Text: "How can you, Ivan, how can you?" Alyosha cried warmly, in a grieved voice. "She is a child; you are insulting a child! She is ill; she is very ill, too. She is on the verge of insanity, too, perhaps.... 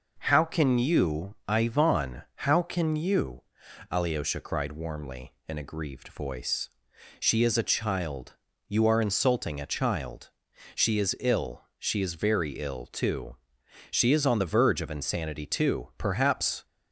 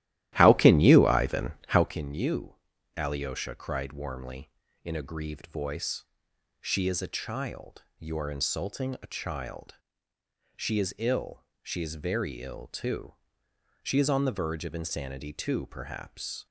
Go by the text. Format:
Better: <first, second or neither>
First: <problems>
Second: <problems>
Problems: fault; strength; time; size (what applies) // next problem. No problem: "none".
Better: first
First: none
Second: starts louder than the rest; strong; until 1.9 s; 14 dB